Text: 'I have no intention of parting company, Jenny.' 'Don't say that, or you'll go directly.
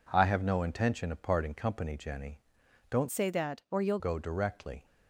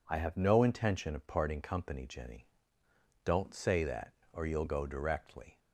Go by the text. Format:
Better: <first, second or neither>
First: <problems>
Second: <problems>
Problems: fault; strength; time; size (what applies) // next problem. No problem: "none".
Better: second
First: changes voice from "say" to "you'll"; from 3.0 to 3.9 s; 0.9 s long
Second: none